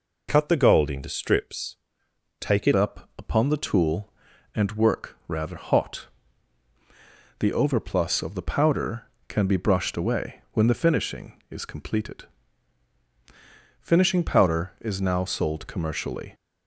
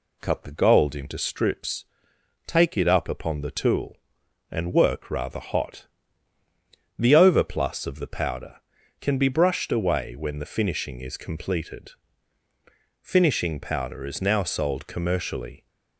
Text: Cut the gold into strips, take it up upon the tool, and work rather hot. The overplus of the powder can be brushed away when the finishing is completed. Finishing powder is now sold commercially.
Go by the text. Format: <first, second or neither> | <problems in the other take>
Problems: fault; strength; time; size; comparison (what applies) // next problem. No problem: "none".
second | changes voice at "up"; from 2.7 s on; 13.6 s long